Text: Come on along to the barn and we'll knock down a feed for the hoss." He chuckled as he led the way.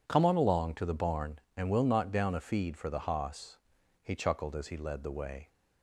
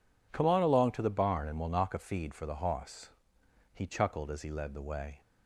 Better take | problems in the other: first | skips "down"; at 1.9 s

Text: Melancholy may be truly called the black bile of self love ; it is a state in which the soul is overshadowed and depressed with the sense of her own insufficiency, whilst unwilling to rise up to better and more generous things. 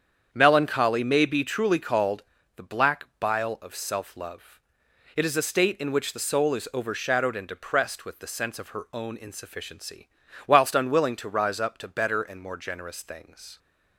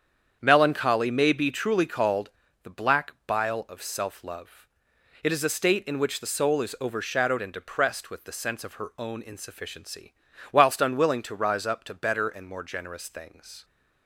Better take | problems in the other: neither | starts louder than the rest; strong; the same in both // pauses between "called" and "the"; slight; the same in both

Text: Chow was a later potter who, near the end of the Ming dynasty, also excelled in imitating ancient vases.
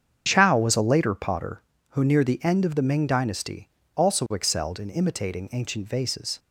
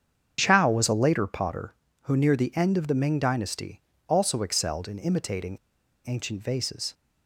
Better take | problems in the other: first | starts louder than the rest; strong; until 1.4 s; 7.5 dB; strong in the first // pauses between "imitating" and "ancient"; noticeable; at 5.5 s; 0.48 s long

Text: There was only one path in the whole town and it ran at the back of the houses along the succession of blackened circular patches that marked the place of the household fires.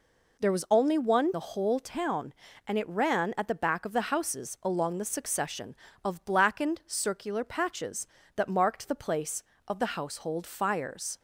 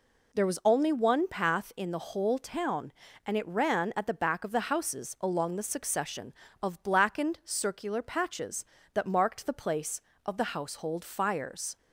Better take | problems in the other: second | skips "path in"; at 1.3 s

